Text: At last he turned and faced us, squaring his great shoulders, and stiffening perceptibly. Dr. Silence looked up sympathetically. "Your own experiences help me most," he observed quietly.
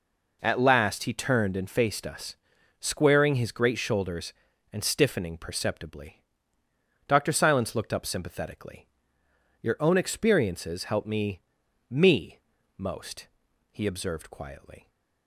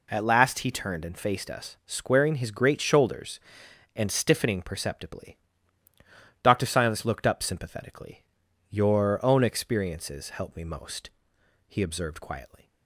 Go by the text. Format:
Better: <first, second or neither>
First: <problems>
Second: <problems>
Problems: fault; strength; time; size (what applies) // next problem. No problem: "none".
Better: second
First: says "me" twice; at 11.8 s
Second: none